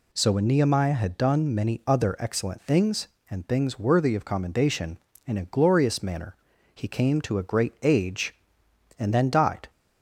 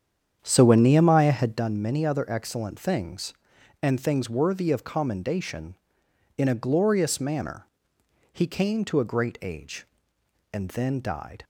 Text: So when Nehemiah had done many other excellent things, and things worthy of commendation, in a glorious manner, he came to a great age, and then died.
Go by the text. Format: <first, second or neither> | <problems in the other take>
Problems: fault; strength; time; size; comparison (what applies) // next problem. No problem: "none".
first | starts louder than the rest; strong; until 1.6 s; 8.5 dB